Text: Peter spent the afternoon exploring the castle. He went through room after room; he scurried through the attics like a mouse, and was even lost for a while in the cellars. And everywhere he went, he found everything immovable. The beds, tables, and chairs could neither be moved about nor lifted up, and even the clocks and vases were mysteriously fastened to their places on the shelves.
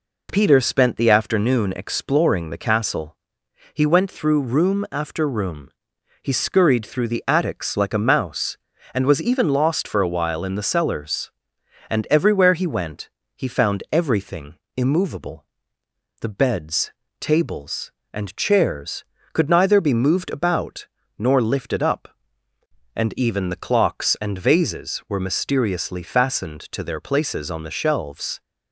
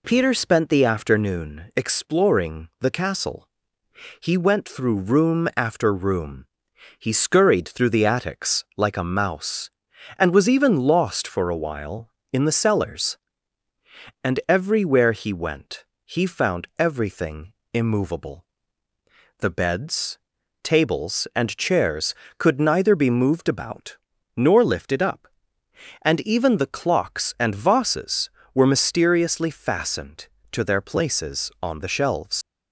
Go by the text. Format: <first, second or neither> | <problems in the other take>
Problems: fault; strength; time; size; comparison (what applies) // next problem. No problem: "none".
first | pauses between "everything" and "immovable"; slight; at 17.5 s; 0.22 s long; slight in the first // pauses between "about" and "nor"; at 23.9 s; 0.38 s long; slight in the first // leaves "shelves" unfinished; at 32.4 s; 100 ms